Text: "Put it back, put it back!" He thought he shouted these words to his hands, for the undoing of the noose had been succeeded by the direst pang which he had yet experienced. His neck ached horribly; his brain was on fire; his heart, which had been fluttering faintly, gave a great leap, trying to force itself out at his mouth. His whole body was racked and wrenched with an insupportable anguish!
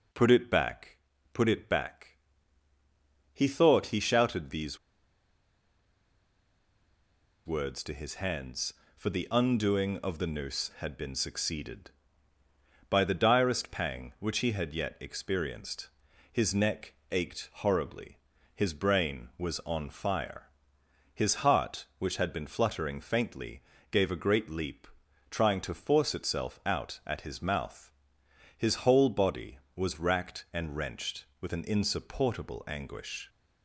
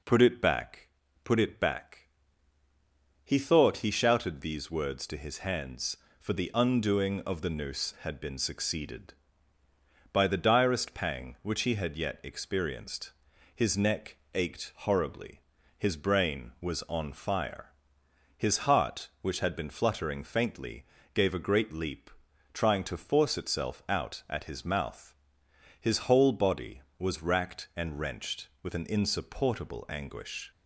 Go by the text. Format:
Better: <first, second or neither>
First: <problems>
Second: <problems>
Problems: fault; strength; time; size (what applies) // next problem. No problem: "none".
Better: second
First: pauses between "these" and "words"; strong; at 4.7 s; 2.6 s long // pauses between "neck" and "ached"; slight; at 16.9 s; 0.18 s long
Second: pauses between "neck" and "ached"; slight; at 14.1 s; 0.18 s long